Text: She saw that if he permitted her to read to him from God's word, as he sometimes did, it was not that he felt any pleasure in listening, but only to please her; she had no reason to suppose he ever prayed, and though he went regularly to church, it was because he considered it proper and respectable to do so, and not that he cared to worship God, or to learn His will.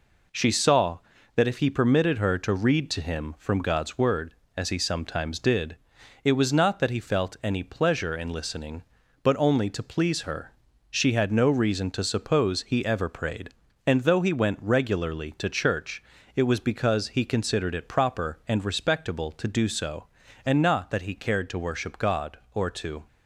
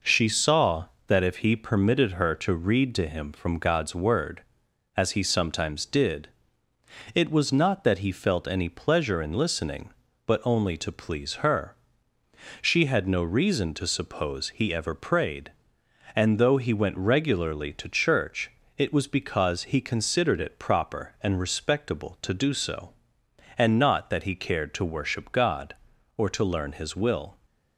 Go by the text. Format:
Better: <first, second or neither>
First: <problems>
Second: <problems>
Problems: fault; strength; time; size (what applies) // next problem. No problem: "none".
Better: second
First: stops before "learn His will"; at 23.0 s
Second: none